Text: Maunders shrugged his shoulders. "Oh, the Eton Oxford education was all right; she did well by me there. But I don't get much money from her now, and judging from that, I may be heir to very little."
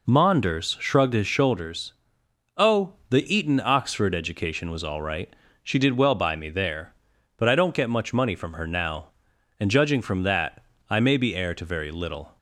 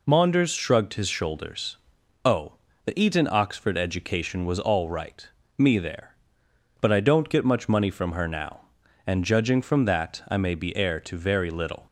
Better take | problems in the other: first | skips "she did well by"; at 5.4 s

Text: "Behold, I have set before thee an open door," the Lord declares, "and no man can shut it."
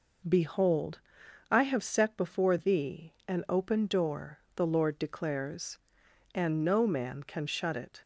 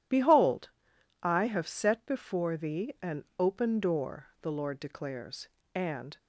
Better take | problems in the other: first | stops before "no man can shut it"; at 6.1 s

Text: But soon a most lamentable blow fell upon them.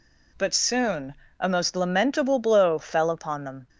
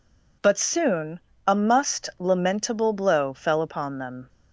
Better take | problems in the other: first | pauses between "soon" and "a"; slight; at 1.1 s; 0.30 s long; slight in the first // says "must" for "most"; at 1.5 s

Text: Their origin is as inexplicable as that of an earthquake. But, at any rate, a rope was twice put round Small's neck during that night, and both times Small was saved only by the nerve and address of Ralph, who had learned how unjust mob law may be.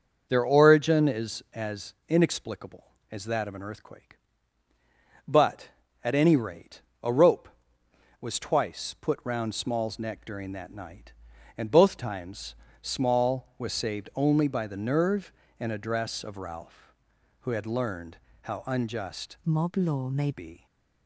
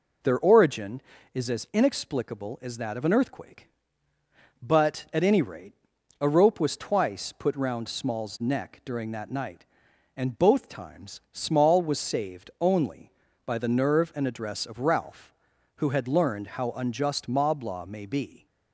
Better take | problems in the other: second | starts louder than the rest; until 1.3 s; 6.5 dB // pauses between "times" and "Small"; slight; at 12.5 s; 0.26 s long // pauses between "learned" and "how"; slight; at 18.1 s; 0.24 s long // changes voice from "mob" to "may"; from 19.4 to 20.3 s; 0.9 s long

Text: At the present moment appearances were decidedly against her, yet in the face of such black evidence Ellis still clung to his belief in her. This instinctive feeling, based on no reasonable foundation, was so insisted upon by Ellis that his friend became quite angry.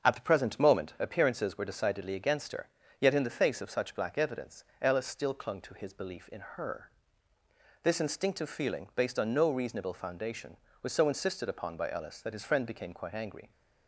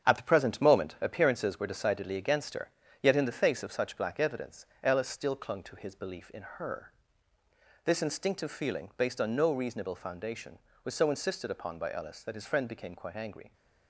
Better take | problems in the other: first | gets quieter; throughout; 6.5 dB // starts louder than the rest; strong; until 1.1 s; 8 dB; also in the first // pauses between "evidence" and "Ellis"; slight; at 4.6 s; 0.16 s long; slight in the first

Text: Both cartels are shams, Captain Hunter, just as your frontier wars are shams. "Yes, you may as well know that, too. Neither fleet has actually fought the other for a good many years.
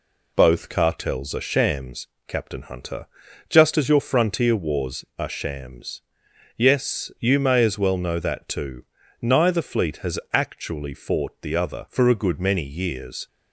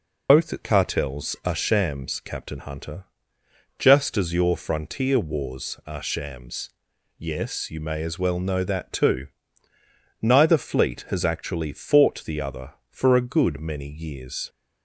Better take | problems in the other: first | loses the start of "Both"; at 0.2 s; 110 ms

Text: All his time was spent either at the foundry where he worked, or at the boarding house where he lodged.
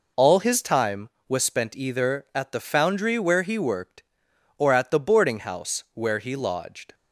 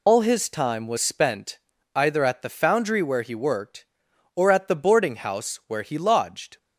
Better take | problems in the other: first | loses the start of "All"; at 0.0 s; 75 ms // pauses between "spent" and "either"; at 1.5 s; 0.38 s long

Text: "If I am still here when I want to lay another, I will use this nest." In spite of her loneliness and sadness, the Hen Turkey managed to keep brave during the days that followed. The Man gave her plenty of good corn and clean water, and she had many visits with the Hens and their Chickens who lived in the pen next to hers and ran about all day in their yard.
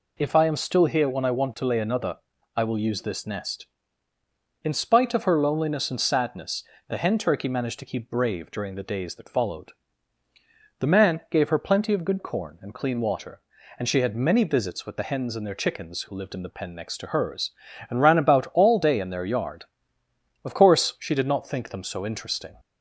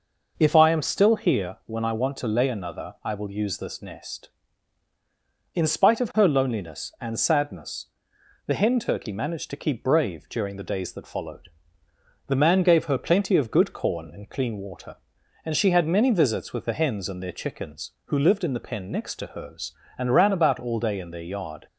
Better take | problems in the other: second | goes on to say "Of course she did not think them so interesting"; strong; from 20.4 s on; 2.1 s long

